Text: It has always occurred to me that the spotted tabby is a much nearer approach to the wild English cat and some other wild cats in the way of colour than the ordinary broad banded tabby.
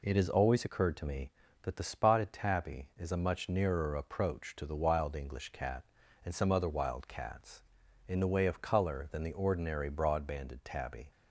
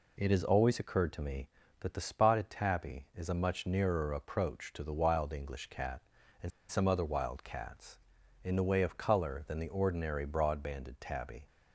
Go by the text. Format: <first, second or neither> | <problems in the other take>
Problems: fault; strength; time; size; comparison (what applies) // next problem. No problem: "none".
first | pauses between "and" and "some"; slight; at 6.5 s; 0.20 s long